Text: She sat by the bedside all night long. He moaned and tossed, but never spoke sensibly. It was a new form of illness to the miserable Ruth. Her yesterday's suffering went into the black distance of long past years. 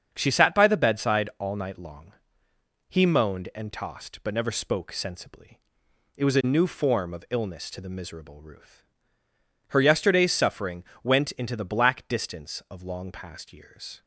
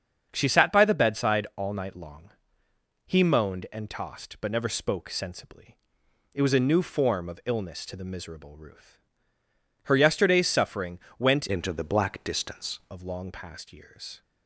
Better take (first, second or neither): first